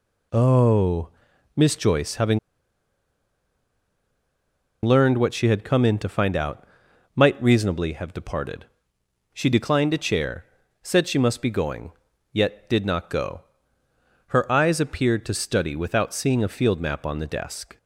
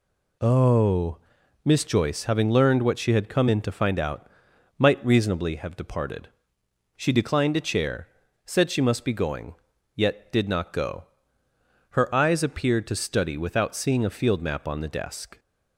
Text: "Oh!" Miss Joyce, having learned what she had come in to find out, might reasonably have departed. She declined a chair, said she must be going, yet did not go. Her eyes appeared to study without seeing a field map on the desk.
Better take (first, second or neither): second